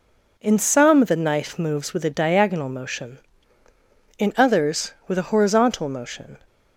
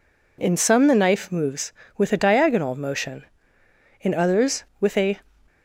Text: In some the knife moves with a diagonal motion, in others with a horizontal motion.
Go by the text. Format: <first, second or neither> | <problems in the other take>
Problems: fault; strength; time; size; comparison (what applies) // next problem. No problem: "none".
first | stops before "horizontal motion"; at 5.4 s